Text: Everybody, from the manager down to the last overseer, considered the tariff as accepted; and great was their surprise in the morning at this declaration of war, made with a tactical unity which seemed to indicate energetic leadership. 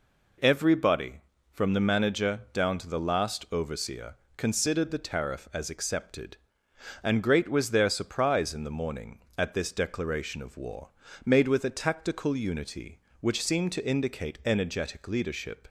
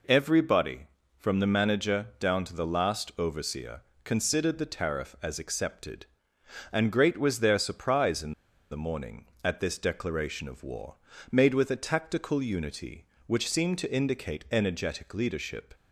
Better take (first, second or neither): first